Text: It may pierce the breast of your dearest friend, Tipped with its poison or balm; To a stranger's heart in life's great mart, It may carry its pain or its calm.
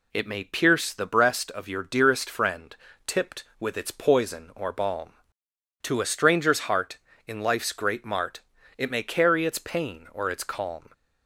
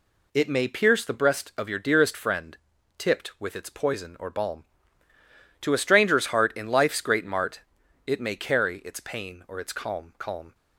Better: first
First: none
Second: says "calm" twice; at 10.1 s

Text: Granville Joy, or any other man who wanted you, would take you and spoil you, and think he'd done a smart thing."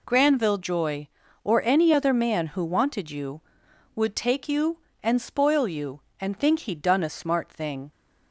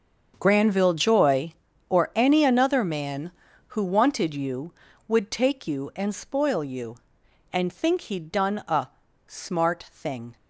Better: first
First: none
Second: starts louder than the rest; until 1.3 s; 6.5 dB // says "another" for "other"; at 2.4 s // pauses between "a" and "smart"; at 8.8 s; 0.40 s long

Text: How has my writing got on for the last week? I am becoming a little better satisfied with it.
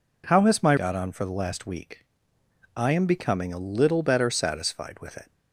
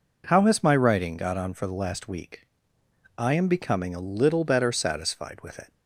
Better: second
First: skips "writing"; at 0.7 s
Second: none

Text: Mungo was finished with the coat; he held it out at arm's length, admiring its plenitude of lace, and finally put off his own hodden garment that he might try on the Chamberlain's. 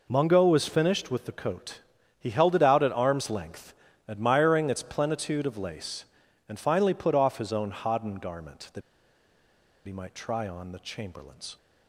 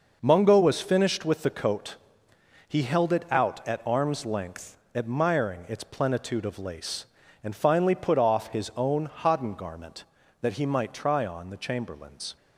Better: second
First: pauses between "that" and "he"; at 8.8 s; 1.0 s long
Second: none

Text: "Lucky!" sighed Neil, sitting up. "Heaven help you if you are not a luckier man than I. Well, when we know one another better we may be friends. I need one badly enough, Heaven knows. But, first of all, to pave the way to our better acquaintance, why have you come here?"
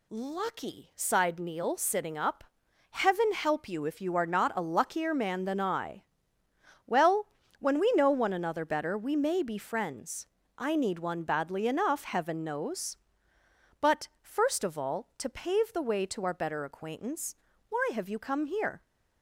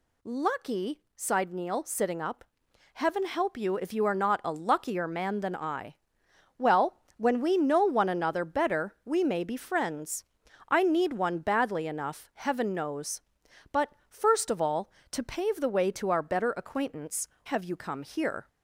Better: first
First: none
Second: skips "why"; at 17.3 s

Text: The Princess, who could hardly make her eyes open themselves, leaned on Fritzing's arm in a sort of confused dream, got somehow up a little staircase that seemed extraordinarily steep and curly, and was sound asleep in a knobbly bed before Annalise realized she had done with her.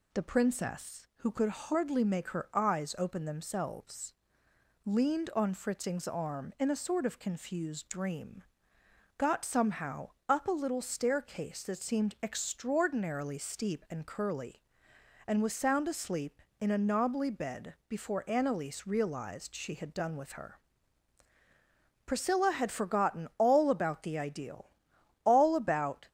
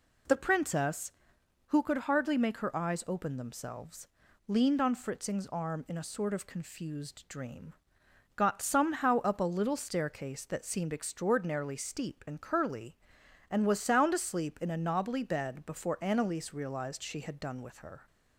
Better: second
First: pauses between "somehow" and "up"; slight; at 10.0 s; 0.20 s long // goes on to say "Priscilla had forgotten all about the Ideal all about"; strong; from 22.0 s on; 4.0 s long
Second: none

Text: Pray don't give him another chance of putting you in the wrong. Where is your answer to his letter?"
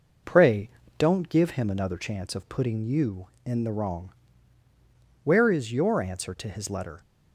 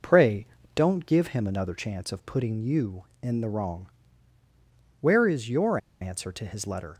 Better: first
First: pauses between "Pray" and "don't"; slight; at 0.6 s; 0.28 s long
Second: pauses between "Pray" and "don't"; slight; at 0.4 s; 0.28 s long // pauses between "your" and "answer"; slight; at 5.7 s; 0.22 s long

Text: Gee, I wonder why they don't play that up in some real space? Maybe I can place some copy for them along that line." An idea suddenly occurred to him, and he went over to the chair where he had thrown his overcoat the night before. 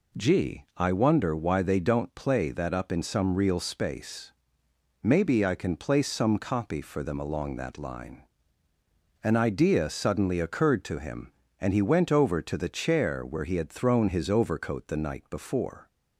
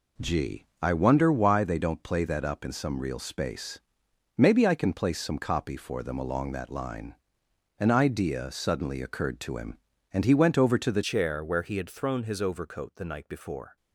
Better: first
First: none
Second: changes voice at "chair"; from 11.0 s on; 2.7 s long

